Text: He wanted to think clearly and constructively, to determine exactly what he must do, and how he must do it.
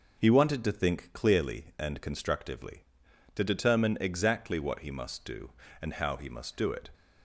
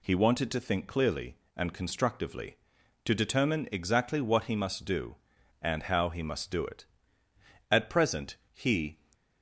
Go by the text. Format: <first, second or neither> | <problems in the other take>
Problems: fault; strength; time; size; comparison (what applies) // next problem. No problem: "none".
first | goes on to say "At present he"; noticeable; from 7.7 s on; 1.2 s long